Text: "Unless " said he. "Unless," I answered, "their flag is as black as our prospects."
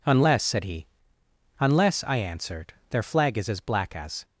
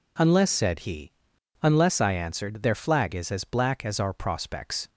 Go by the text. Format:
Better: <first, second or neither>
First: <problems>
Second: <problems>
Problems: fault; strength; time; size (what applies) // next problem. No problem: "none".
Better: second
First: stops before "our prospects"; at 4.2 s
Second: none